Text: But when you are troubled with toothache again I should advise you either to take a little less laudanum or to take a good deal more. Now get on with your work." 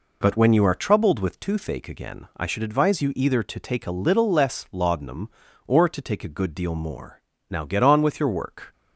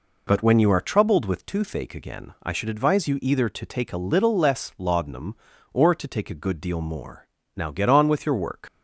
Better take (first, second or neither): first